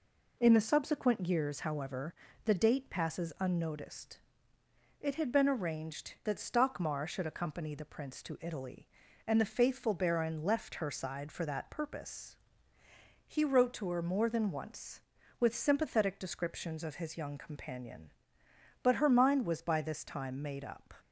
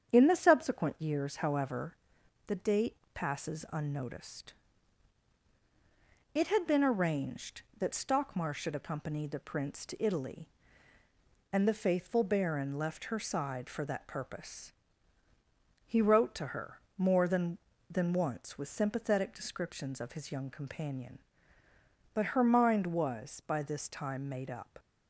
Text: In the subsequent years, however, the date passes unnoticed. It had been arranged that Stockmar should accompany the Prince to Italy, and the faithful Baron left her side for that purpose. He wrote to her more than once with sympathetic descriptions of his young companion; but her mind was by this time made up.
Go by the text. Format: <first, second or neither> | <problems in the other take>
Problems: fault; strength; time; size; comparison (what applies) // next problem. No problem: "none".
first | starts louder than the rest; strong; until 1.1 s; 8 dB // pauses between "date" and "passes"; slight; at 2.9 s; 0.18 s long // pauses between "her" and "more"; slight; at 16.7 s; 0.18 s long // says "than" twice; at 17.9 s